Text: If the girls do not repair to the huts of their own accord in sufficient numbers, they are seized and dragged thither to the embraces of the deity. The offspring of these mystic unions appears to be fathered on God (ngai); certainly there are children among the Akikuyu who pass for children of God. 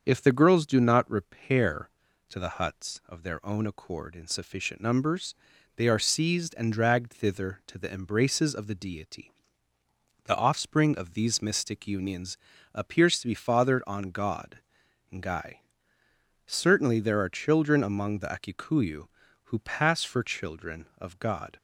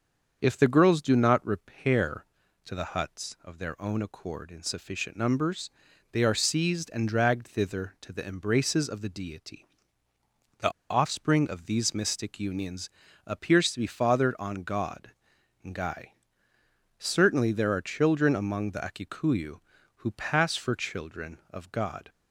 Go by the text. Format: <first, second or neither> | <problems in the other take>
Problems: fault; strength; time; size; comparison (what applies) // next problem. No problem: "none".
first | starts louder than the rest; until 1.4 s; 7 dB; also in the first // pauses between "The" and "offspring"; slight; at 10.7 s; 0.19 s long // pauses between "unions" and "appears"; at 12.8 s; 0.38 s long; also in the first